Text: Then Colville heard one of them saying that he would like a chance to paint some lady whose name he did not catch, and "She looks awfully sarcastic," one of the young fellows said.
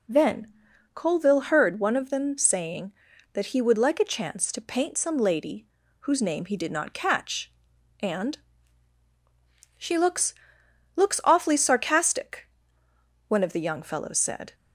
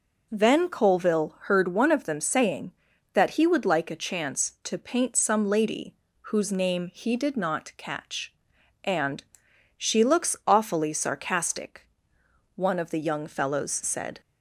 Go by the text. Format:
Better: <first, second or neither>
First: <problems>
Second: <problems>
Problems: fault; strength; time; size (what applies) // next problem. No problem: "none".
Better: second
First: pauses between "Then" and "Colville"; noticeable; at 0.4 s; 0.48 s long // pauses between "lady" and "whose"; slight; at 5.6 s; 0.34 s long // pauses between "and" and "She"; strong; at 8.3 s; 1.4 s long // says "looks" twice; at 10.9 s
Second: pauses between "lady" and "whose"; slight; at 5.9 s; 0.28 s long // pauses between "and" and "She"; noticeable; at 9.2 s; 0.54 s long